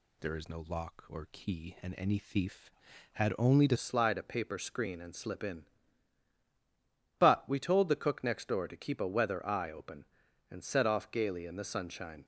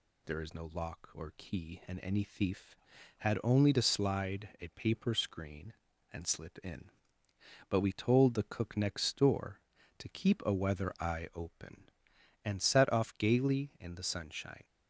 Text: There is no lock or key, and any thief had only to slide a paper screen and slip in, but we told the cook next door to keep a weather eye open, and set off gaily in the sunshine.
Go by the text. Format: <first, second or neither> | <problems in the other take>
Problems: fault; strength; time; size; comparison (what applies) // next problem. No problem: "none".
second | changes voice at "slide"; from 3.7 s on; 8.5 s long